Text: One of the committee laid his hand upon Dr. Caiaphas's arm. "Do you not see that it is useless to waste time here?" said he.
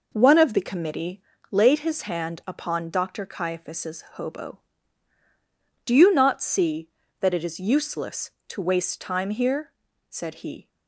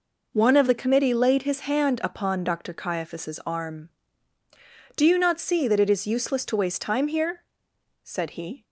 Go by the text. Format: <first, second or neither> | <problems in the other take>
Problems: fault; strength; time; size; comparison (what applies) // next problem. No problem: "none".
second | pauses between "committee" and "laid"; slight; at 1.2 s; 0.28 s long // says "hobo" for "arm"; at 4.1 s